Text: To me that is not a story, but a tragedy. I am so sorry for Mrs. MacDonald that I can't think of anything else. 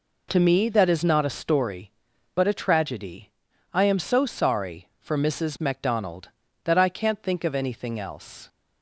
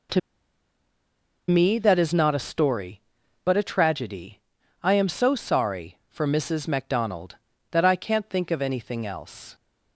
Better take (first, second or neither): first